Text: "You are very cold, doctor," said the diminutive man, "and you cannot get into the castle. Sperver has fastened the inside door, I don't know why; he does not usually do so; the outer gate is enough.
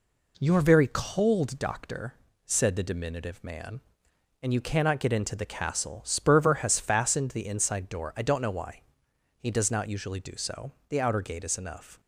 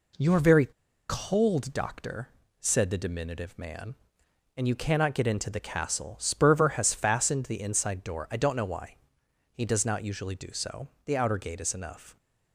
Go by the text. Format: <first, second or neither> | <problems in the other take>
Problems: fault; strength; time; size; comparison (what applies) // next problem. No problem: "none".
first | pauses between "very" and "cold"; at 0.6 s; 0.40 s long